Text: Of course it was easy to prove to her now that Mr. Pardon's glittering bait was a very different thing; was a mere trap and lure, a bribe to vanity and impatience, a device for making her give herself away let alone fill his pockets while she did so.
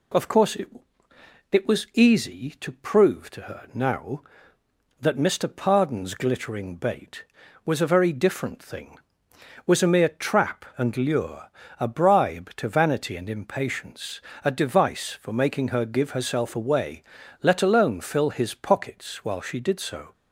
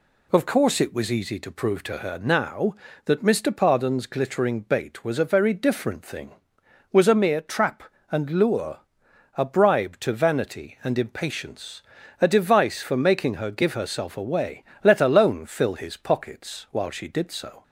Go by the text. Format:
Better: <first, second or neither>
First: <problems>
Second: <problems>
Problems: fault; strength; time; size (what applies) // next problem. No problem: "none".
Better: second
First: says "it" twice; at 1.5 s // pauses between "away" and "let"; at 17.0 s; 0.38 s long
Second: pauses between "away" and "let"; slight; at 14.6 s; 0.20 s long